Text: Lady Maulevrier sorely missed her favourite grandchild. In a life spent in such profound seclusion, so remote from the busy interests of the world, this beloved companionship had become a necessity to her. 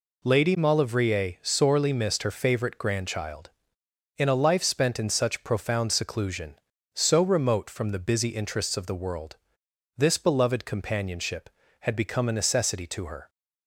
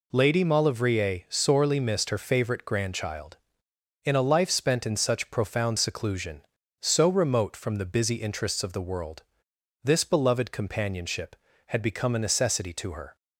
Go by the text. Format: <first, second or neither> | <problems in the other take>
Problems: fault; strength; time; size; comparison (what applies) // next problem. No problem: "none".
neither | none